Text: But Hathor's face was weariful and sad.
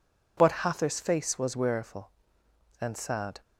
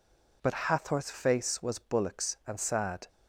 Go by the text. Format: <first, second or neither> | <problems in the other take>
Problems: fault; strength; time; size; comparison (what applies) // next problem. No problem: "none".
first | says "bullocks" for "weariful"; at 1.7 s